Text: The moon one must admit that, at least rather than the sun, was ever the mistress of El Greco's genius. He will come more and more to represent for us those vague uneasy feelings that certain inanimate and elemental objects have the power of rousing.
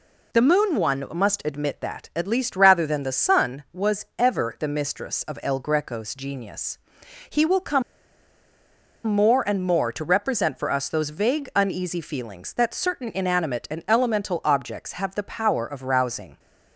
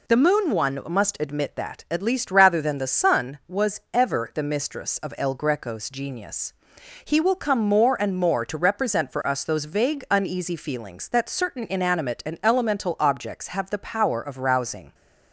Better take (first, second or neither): second